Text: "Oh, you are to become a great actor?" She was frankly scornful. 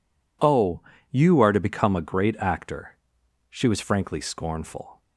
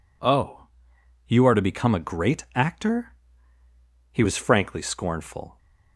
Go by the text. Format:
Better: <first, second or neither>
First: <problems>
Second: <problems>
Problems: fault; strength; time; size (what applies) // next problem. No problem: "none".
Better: first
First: none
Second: says "He" for "She"; at 4.1 s